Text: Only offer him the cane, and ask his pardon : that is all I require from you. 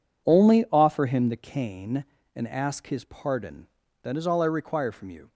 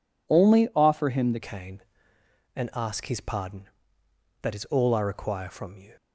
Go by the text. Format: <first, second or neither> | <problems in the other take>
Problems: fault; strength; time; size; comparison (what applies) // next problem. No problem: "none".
first | changes voice at "cane"; from 1.3 s on; 4.6 s long